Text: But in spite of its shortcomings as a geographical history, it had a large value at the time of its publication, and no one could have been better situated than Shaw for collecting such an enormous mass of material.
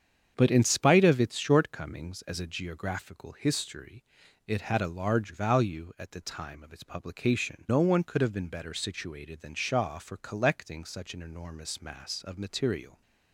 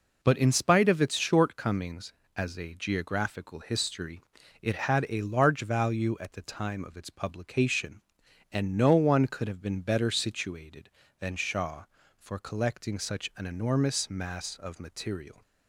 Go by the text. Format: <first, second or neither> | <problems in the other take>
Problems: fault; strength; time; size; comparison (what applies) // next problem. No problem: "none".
second | starts louder than the rest; strong; until 1.3 s; 8 dB // skips "and"; at 7.6 s